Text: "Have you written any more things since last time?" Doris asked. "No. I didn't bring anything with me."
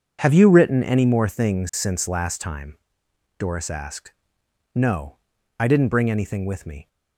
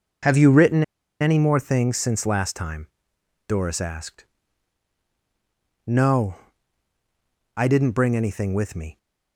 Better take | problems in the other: first | pauses between "written" and "any"; at 0.8 s; 0.38 s long

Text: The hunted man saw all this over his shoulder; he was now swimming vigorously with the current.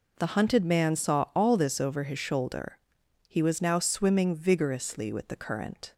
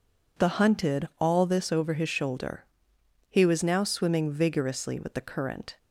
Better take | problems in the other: first | skips "man saw"; at 1.1 s

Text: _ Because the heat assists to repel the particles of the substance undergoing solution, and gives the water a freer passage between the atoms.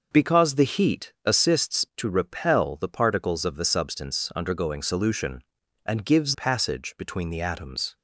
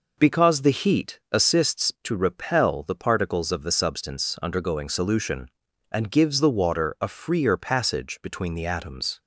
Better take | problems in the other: second | skips "the water a freer"; at 6.3 s

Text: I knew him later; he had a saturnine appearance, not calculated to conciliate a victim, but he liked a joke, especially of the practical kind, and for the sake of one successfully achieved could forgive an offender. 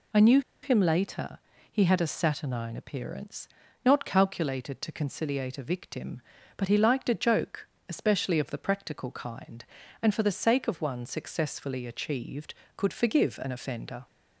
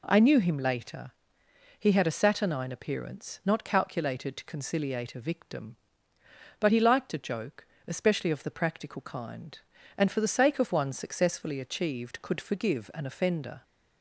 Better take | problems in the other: second | pauses between "knew" and "him"; slight; at 0.3 s; 0.22 s long

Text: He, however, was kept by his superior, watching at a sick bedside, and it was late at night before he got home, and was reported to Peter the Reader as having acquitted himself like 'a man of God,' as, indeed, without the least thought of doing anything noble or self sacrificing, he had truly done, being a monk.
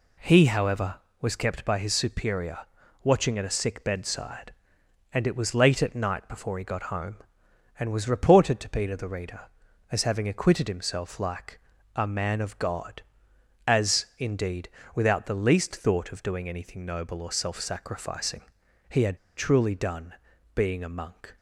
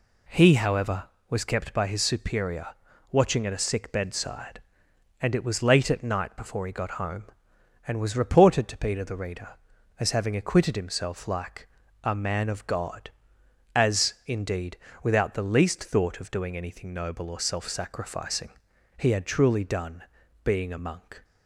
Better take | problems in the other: second | pauses between "like" and "a"; slight; at 11.5 s; 0.36 s long; slight in the second // pauses between "had" and "truly"; slight; at 19.1 s; 0.19 s long

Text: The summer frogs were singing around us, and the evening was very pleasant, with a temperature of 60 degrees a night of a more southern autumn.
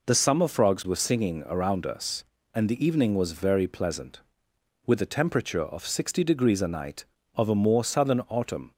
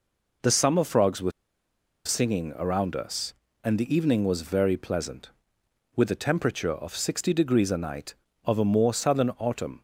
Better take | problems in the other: first | pauses between "were" and "singing"; noticeable; at 1.3 s; 0.74 s long

